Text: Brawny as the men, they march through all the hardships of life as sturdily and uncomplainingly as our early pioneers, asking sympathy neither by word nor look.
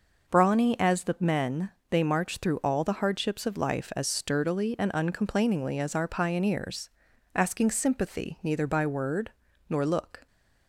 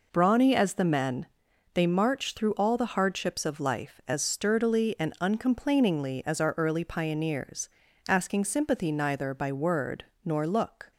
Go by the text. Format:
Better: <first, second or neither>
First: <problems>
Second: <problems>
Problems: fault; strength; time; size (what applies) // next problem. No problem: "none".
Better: second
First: skips "early"; at 6.0 s // pauses between "word" and "nor"; at 9.3 s; 0.38 s long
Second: pauses between "word" and "nor"; slight; at 10.0 s; 0.20 s long